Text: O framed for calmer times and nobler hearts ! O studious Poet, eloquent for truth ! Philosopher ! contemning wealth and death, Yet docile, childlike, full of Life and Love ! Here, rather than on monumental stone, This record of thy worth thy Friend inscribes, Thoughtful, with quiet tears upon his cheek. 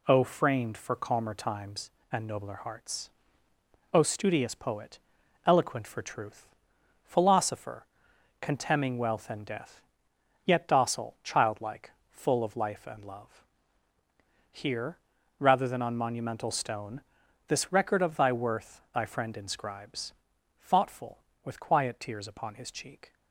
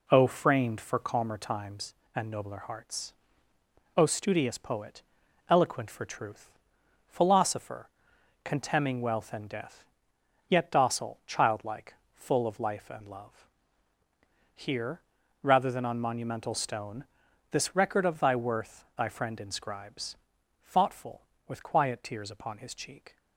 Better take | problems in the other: first | starts louder than the rest; slight; until 1.1 s; 2.5 dB

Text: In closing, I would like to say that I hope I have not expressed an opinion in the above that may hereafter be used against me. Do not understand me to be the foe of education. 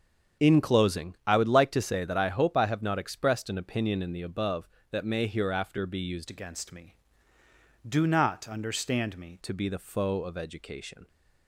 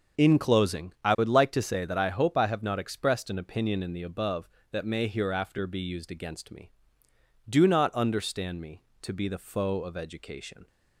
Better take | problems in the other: second | starts louder than the rest; until 1.5 s; 7 dB; also in the second // changes voice from "against" to "me"; from 6.2 to 9.3 s; 3.1 s long

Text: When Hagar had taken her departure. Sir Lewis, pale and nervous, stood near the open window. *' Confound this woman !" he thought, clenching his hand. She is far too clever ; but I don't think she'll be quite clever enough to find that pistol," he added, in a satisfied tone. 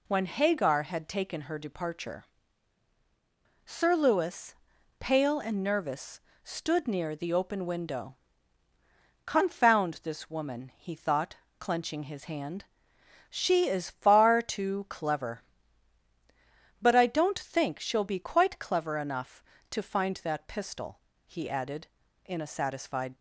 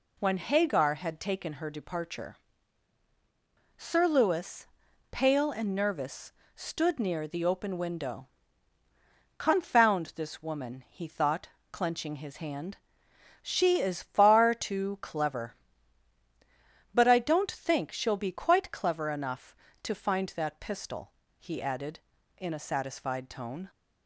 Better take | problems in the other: second | stops before "tone"; at 23.1 s

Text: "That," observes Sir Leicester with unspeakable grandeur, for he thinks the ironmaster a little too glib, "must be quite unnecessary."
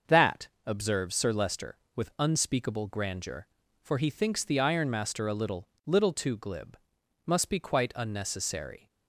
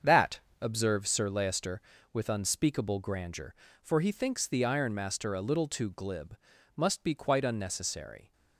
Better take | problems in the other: second | starts louder than the rest; until 1.2 s; 6.5 dB; also in the second // says "little" twice; at 5.8 s

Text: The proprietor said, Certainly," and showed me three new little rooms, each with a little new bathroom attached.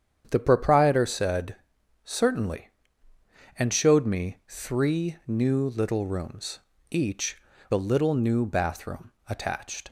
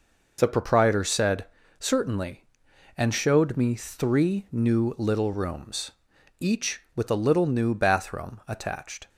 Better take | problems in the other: second | starts louder than the rest; strong; until 1.3 s; 8.5 dB // skips "with"; at 7.5 s // pauses between "bathroom" and "attached"; slight; at 9.1 s; 0.16 s long

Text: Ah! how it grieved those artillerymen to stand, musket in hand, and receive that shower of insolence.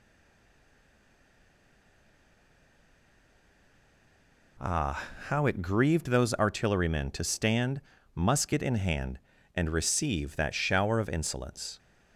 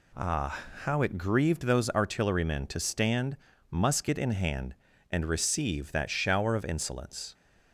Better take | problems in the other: second | stays silent before the first word; strong; until 4.5 s; 4.5 s long

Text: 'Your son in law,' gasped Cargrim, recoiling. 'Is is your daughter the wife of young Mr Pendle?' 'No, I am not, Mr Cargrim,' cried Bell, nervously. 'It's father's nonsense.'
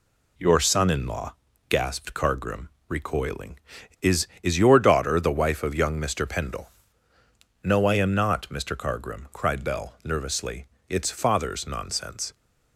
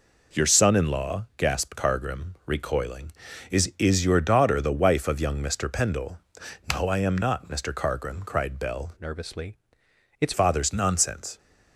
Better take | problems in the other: first | changes voice from "nervously" to "It's"; from 9.0 to 10.3 s; 1.3 s long

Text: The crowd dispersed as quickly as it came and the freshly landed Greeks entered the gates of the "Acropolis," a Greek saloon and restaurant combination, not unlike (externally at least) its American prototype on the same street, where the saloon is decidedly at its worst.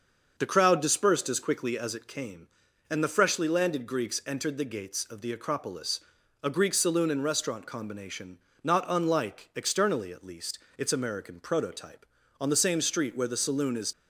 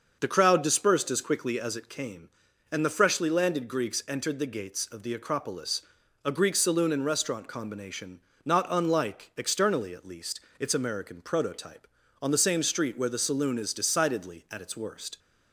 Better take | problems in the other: second | starts louder than the rest; until 1.3 s; 6.5 dB; also in the second // stops before "decidedly at its worst"; at 13.9 s

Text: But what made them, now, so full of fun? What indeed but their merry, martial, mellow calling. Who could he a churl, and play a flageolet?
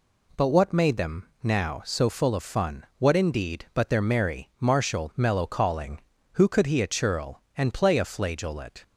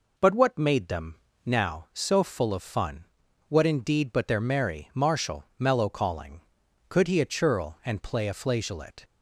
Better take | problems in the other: first | skips "Who"; at 6.6 s

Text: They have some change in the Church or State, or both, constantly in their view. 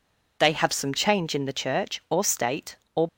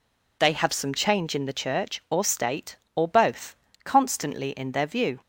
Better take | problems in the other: second | stops before "both constantly in their view"; at 3.0 s

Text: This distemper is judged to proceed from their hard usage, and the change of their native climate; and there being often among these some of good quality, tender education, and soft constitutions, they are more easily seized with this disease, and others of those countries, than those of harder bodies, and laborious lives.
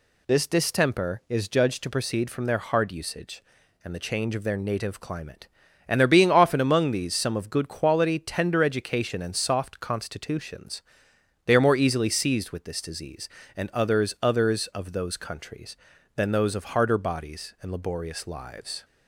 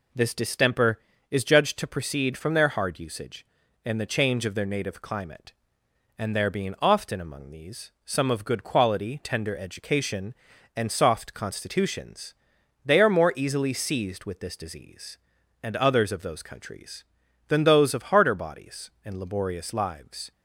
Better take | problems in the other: second | says "others" twice; at 14.2 s

